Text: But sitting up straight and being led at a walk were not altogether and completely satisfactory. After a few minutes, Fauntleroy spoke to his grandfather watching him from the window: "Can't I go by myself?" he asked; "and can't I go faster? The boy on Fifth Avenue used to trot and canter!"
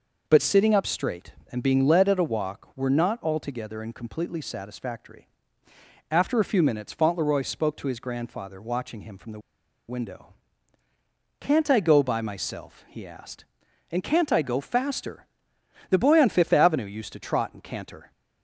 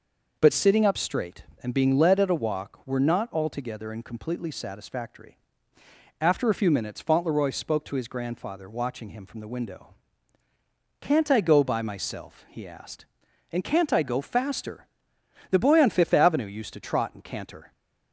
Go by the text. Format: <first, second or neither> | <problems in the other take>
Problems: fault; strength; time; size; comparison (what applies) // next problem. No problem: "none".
second | pauses between "the" and "window"; noticeable; at 9.3 s; 0.49 s long